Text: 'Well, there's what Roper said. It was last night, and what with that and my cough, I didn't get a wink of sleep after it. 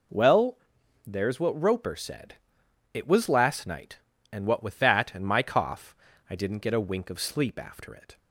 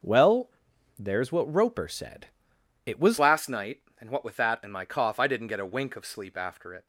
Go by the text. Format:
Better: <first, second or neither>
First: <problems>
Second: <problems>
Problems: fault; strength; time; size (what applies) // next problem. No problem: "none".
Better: first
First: none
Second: changes voice at "last"; from 3.1 s on; 3.7 s long